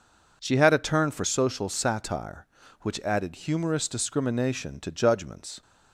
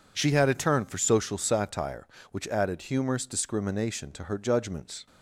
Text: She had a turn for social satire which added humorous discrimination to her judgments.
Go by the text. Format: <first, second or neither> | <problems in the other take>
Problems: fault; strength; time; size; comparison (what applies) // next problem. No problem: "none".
second | skips "her"; at 4.9 s